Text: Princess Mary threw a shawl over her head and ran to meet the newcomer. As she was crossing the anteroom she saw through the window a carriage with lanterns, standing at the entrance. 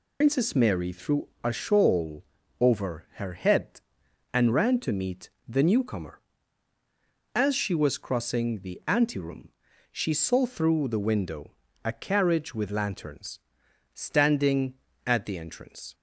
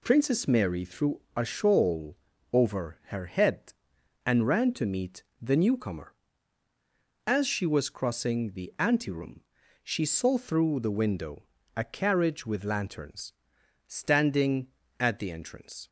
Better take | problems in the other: second | loses the start of "Princess"; at 0.2 s; 95 ms // pauses between "shawl" and "over"; slight; at 2.2 s; 0.34 s long; slight in the second // pauses between "meet" and "the"; slight; at 5.2 s; 0.18 s long; slight in the second // pauses between "anteroom" and "she"; at 9.4 s; 0.42 s long; also in the second // pauses between "window" and "a"; slight; at 11.5 s; 0.32 s long; slight in the second

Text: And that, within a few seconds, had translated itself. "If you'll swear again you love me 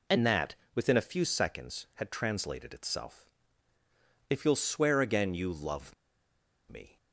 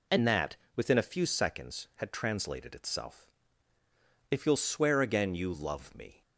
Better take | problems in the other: second | pauses between "love" and "me"; noticeable; at 5.9 s; 0.76 s long

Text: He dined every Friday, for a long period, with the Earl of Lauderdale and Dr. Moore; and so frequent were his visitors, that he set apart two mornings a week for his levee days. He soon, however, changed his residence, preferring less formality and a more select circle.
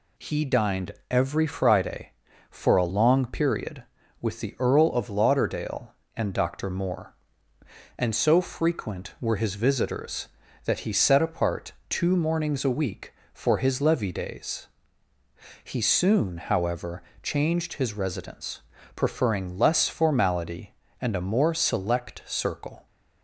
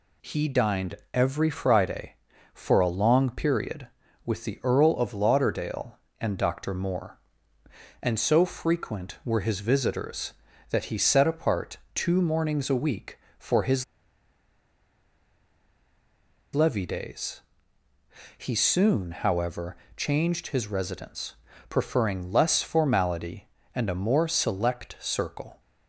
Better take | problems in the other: first | pauses between "dined" and "every"; slight; at 0.9 s; 0.18 s long; slight in the first // pauses between "apart" and "two"; slight; at 11.7 s; 0.18 s long; slight in the first // pauses between "his" and "levee"; strong; at 13.8 s; 2.7 s long

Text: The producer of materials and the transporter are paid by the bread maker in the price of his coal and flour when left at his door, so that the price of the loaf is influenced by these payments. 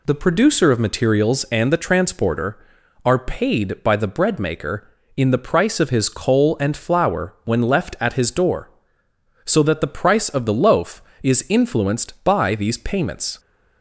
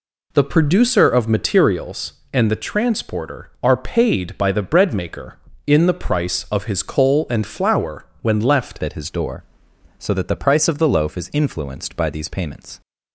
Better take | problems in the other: first | changes voice at "at"; from 8.8 s on; 4.0 s long

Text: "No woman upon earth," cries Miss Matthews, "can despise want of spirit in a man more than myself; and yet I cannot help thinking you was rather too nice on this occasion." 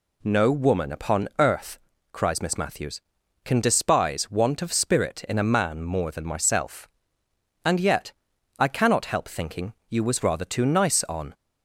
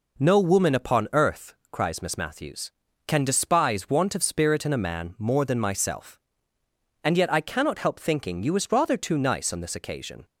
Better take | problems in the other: second | pauses between "yet" and "I"; noticeable; at 8.1 s; 0.48 s long // pauses between "thinking" and "you"; slight; at 9.7 s; 0.16 s long // stops before "this occasion"; at 11.3 s

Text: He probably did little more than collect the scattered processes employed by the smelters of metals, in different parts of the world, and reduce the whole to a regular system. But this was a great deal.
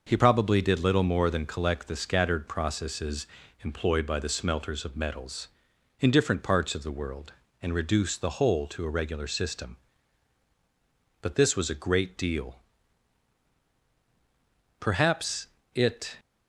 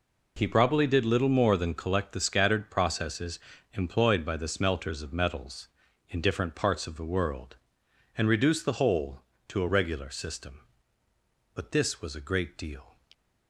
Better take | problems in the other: second | pauses between "processes" and "employed"; at 3.2 s; 0.38 s long; slight in the second // goes on to say "Perhaps it"; from 14.7 s on; 1.3 s long

